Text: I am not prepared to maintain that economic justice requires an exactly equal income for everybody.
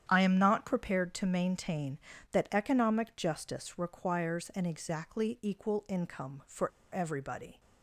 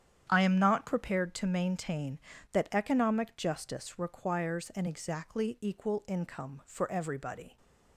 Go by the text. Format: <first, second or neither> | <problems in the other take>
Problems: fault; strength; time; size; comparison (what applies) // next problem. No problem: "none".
second | starts louder than the rest; strong; until 1.0 s; 9.5 dB; strong in the second // pauses between "for" and "everybody"; slight; at 6.7 s; 0.23 s long